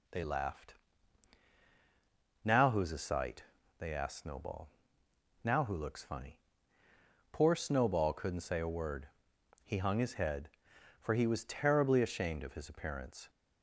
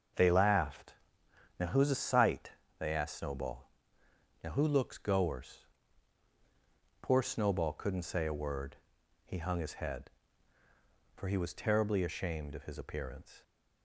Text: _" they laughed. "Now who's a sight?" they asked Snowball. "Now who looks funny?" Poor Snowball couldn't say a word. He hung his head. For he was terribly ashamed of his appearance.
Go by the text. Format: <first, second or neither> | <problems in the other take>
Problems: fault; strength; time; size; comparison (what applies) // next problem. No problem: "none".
first | starts louder than the rest; until 1.7 s; 6.5 dB // says "goers" for "funny"; at 4.9 s